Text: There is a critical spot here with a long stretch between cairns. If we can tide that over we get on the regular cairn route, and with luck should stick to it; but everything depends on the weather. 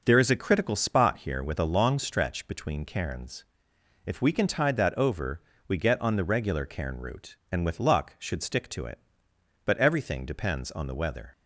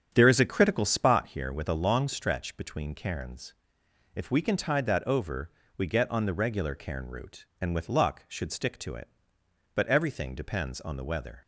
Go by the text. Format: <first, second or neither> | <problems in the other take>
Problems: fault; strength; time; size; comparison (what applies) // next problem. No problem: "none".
first | starts louder than the rest; strong; until 1.2 s; 8.5 dB // pauses between "over" and "we"; slight; at 5.5 s; 0.28 s long; slight in the first